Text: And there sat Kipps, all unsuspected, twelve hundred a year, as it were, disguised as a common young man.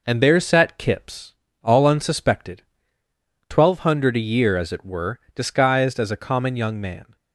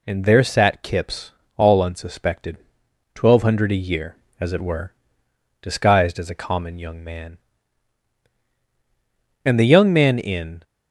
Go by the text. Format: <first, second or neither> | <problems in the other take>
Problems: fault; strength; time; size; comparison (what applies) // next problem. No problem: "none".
first | goes on to say "And the young man in"; noticeable; from 9.4 s on; 1.1 s long